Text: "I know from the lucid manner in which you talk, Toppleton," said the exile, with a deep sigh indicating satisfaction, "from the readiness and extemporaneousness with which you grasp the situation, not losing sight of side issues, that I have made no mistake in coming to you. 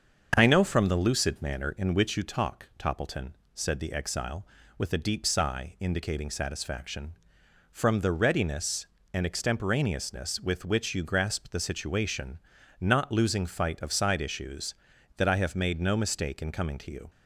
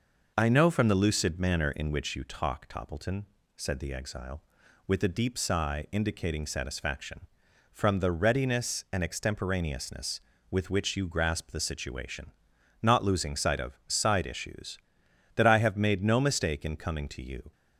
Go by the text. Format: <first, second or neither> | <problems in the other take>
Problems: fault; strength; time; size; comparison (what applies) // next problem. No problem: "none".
second | starts louder than the rest; until 1.3 s; 7 dB // says "fight" for "sight"; at 13.4 s